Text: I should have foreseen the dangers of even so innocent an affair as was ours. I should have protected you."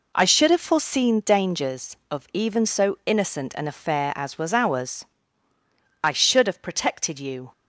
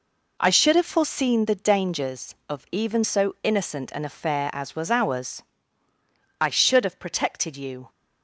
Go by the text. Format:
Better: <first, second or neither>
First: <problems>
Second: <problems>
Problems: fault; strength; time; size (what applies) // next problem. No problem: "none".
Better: second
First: skips "the"; at 1.2 s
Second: none